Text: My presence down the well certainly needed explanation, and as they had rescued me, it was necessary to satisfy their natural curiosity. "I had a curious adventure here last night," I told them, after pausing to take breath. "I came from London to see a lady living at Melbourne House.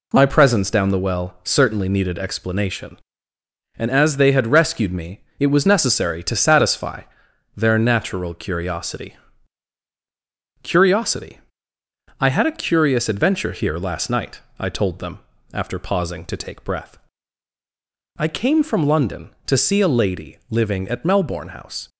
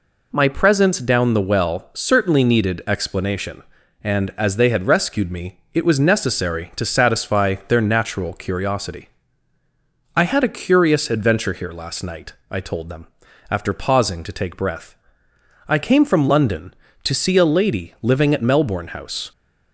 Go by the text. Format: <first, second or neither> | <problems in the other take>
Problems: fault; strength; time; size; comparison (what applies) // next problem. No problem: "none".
second | pauses between "satisfy" and "their"; noticeable; at 7.0 s; 0.54 s long // says "curiosity" twice; at 10.6 s